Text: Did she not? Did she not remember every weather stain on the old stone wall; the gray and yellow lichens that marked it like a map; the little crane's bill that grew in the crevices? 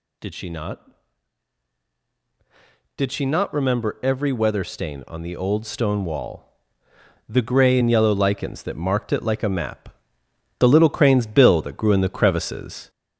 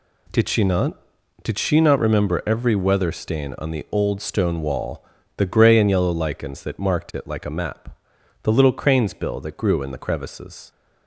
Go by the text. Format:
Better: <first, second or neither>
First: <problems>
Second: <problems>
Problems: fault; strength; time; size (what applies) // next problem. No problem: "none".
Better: second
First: gets louder; slight; throughout; 2.5 dB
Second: none